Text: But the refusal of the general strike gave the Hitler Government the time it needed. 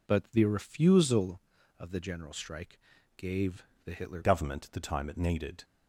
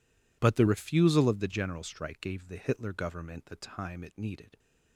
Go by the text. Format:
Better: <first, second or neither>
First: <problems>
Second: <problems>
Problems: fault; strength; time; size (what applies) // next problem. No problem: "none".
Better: second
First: pauses between "strike" and "gave"; at 2.7 s; 0.38 s long // pauses between "gave" and "the"; slight; at 3.6 s; 0.20 s long // changes voice at "Government"; from 4.2 s on; 1.4 s long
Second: none